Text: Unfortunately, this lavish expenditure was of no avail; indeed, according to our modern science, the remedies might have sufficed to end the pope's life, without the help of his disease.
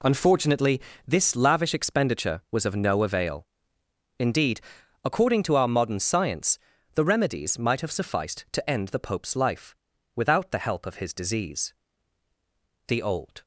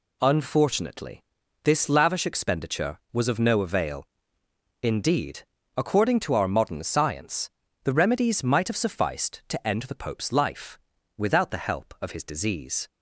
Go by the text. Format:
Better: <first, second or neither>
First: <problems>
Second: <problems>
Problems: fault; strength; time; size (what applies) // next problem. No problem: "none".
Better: second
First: goes on to say "The old"; from 12.8 s on; 0.56 s long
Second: none